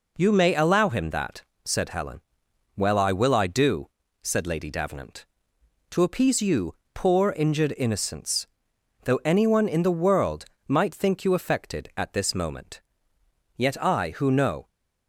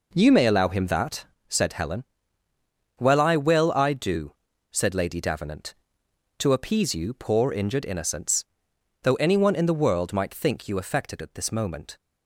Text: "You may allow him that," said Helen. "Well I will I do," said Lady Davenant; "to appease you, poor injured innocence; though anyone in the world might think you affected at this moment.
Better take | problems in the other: second | pauses between "world" and "might"; slight; at 10.4 s; 0.22 s long // goes on to say "Yet I who know"; noticeable; from 13.5 s on; 1.1 s long

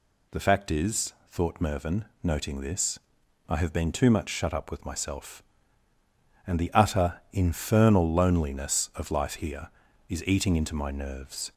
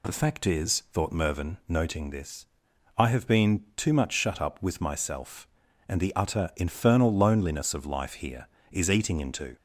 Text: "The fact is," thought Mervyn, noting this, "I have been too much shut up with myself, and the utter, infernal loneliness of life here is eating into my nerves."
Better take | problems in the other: first | stops before "my nerves"; at 9.5 s

